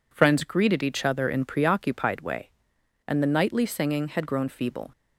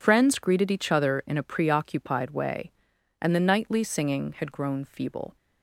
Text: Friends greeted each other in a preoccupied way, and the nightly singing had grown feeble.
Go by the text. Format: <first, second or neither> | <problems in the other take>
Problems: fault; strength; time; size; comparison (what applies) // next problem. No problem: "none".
second | skips "a"; at 1.4 s